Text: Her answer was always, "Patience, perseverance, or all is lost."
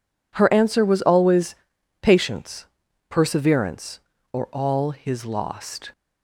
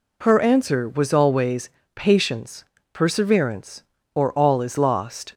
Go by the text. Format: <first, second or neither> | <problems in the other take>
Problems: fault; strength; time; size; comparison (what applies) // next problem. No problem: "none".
second | says "his" for "is"; at 4.8 s